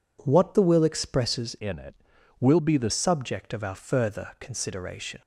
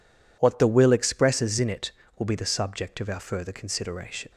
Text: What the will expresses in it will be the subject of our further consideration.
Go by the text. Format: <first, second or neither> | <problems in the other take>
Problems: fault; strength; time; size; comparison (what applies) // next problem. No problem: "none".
second | changes voice from "in" to "the"; from 1.5 to 2.9 s; 1.4 s long